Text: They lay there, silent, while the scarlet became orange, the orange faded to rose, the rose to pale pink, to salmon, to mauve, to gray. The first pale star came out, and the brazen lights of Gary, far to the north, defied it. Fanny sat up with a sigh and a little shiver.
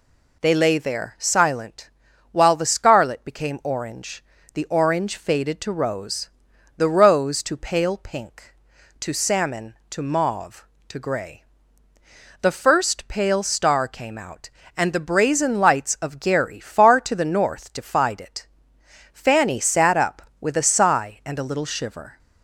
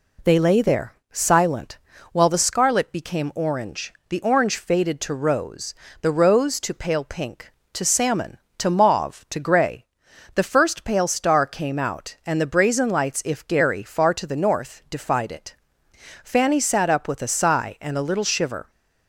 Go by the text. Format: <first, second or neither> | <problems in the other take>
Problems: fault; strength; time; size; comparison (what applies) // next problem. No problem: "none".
first | says "if" for "of"; at 13.2 s